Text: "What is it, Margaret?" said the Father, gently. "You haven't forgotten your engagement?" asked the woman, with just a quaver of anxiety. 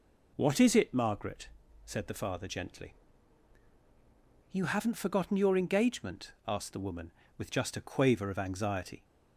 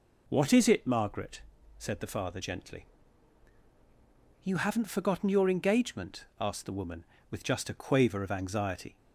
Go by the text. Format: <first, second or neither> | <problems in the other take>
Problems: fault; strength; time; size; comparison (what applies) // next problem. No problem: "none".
neither | none